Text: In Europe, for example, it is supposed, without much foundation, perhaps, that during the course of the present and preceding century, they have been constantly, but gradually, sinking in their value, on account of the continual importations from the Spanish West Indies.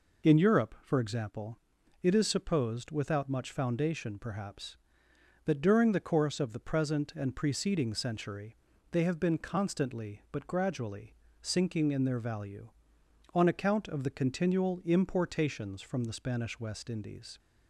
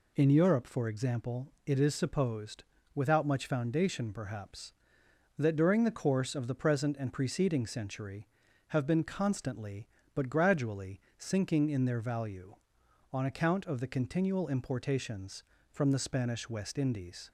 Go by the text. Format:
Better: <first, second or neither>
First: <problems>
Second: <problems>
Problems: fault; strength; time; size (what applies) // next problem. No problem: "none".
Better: first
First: none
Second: skips "they"; at 8.4 s